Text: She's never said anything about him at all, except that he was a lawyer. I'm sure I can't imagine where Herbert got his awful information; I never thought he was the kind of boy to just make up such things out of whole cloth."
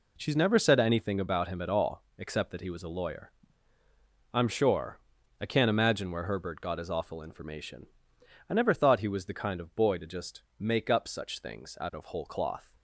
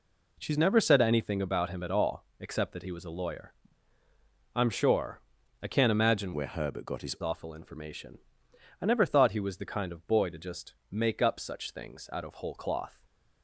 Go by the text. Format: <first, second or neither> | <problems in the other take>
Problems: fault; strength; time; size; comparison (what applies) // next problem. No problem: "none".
first | pauses between "sure" and "I"; at 5.2 s; 0.40 s long; also in the first // changes voice from "where" to "his"; from 6.3 to 7.1 s; 0.8 s long // pauses between "just" and "make"; slight; at 10.7 s; 0.18 s long; slight in the first // stays silent after the last word; slight; from 12.9 s on; 0.5 s long